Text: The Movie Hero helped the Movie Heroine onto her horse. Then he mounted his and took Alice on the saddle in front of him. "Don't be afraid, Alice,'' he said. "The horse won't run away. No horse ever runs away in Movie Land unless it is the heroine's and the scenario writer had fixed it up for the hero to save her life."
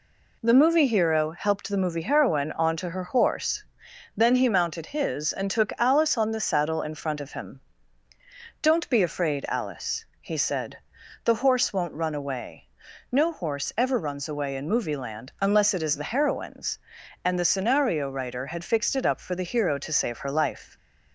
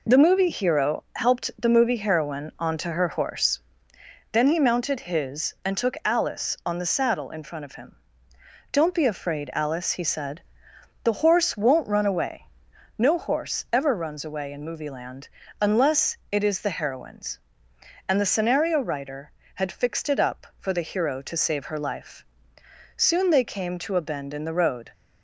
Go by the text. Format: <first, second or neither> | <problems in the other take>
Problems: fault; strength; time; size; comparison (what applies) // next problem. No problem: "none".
first | pauses between "Land" and "unless"; slight; at 15.2 s; 0.32 s long // pauses between "unless" and "it"; slight; at 16.1 s; 0.16 s long // goes on to say "Soon they came to a bend in the road"; strong; from 22.9 s on; 1.9 s long